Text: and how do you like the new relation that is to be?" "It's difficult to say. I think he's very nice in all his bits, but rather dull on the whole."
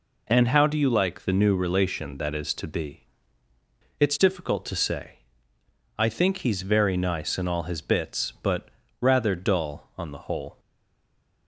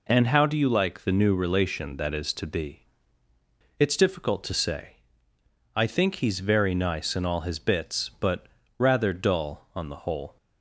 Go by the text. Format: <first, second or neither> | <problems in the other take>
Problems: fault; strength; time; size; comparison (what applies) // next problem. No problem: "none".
second | pauses between "but" and "rather"; slight; at 8.6 s; 0.32 s long; slight in the second // stays silent after the last word; slight; from 10.5 s on; 0.9 s long